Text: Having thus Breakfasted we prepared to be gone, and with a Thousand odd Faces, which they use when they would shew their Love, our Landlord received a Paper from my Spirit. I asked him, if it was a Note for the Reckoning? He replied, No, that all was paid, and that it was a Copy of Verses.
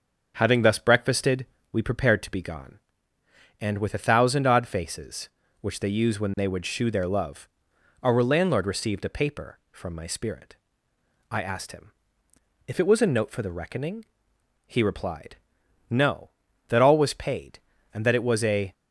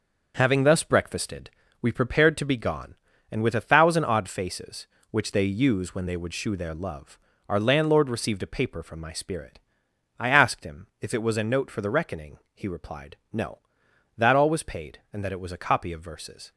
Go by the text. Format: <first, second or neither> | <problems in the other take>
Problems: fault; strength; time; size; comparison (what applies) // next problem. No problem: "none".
second | starts louder than the rest; until 1.3 s; 6.5 dB; noticeable in the second // pauses between "Breakfasted" and "we"; slight; at 1.4 s; 0.26 s long; slight in the second // stops before "Copy of Verses"; at 18.7 s